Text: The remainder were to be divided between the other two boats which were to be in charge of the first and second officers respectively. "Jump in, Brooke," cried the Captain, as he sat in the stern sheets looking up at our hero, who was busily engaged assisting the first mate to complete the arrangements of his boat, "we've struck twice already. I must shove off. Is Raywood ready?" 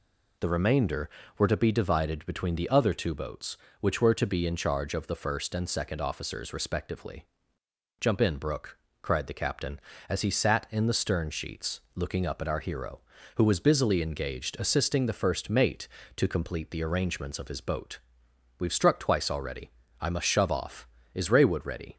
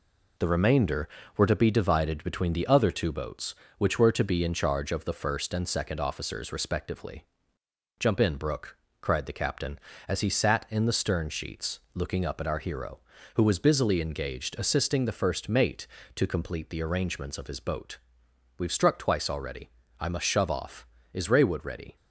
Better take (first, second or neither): first